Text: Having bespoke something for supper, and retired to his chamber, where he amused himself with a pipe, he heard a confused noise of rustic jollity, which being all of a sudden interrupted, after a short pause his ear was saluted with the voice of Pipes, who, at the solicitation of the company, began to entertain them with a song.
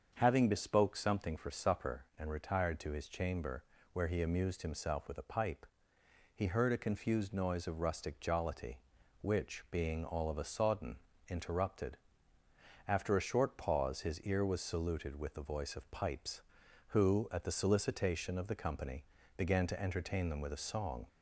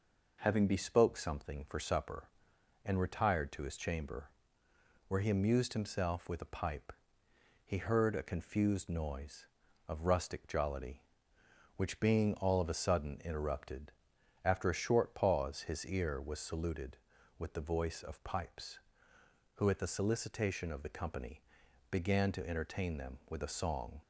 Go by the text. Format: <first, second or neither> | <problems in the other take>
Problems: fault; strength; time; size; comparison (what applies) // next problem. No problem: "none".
second | starts louder than the rest; until 1.1 s; 7 dB // says "sodden" for "sudden"; at 10.4 s